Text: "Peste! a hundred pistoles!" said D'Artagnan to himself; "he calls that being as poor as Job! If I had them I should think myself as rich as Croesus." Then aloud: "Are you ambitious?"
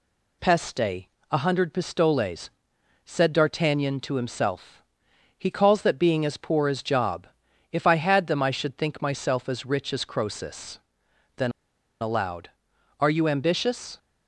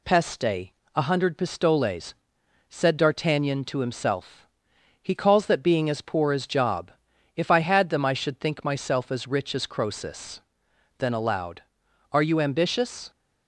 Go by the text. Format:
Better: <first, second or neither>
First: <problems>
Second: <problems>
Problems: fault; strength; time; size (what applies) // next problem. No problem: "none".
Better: second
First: pauses between "Then" and "aloud"; noticeable; at 11.5 s; 0.50 s long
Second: none